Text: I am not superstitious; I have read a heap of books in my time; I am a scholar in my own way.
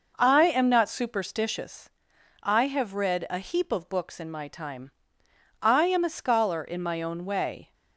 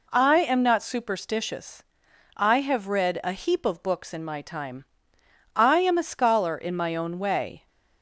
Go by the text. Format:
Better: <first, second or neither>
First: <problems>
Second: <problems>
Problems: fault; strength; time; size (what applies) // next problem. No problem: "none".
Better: second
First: starts louder than the rest; noticeable; until 1.8 s; 5.5 dB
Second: none